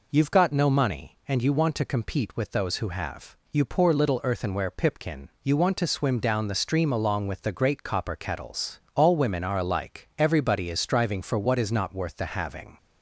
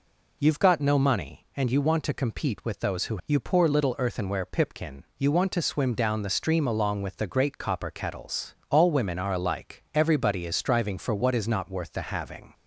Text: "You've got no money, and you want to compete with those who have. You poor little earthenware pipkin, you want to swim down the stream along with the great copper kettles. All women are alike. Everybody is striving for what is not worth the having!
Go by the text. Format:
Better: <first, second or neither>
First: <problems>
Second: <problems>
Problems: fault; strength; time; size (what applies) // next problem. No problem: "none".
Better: first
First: none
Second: skips "have"; at 3.2 s